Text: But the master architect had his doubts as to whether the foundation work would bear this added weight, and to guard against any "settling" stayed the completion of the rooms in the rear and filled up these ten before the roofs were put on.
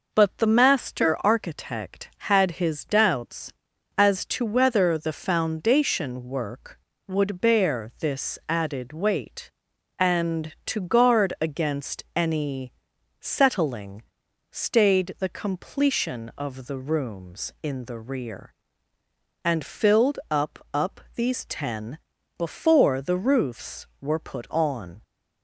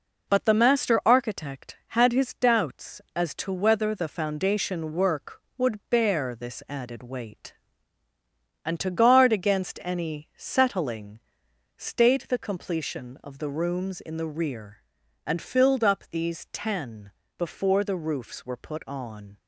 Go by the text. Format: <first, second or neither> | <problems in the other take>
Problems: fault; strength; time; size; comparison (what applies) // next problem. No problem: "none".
second | pauses between "any" and "settling"; noticeable; at 12.7 s; 0.48 s long // pauses between "settling" and "stayed"; noticeable; at 14.0 s; 0.46 s long; noticeable in the second // says "up" twice; at 20.7 s // pauses between "ten" and "before"; at 21.9 s; 0.40 s long; slight in the second